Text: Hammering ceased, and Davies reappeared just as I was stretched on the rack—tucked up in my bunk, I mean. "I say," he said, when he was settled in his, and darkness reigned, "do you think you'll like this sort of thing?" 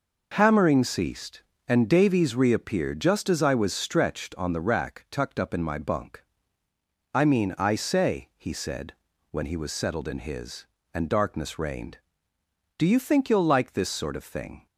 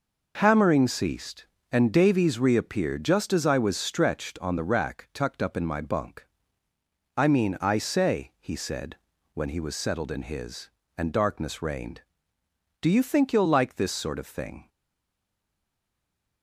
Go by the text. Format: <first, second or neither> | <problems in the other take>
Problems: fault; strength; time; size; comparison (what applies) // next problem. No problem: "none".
first | stays silent after the last word; noticeable; from 14.6 s on; 1.8 s long